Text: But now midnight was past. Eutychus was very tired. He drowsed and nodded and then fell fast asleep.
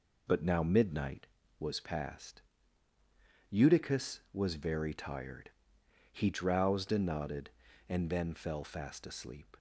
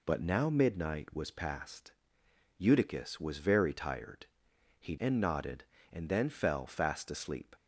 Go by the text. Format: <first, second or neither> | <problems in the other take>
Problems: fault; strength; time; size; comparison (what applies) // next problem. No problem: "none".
first | skips "drowsed"; at 4.9 s